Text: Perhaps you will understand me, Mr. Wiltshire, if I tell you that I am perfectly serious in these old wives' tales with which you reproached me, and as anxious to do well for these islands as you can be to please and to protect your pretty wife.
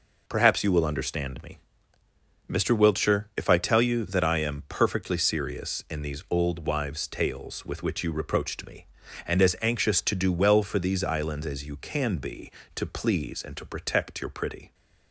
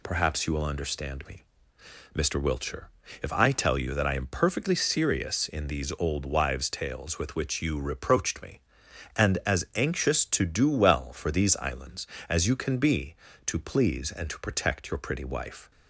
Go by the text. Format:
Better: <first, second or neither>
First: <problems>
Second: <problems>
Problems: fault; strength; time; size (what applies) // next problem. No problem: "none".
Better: second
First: stops before "wife"; at 14.7 s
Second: none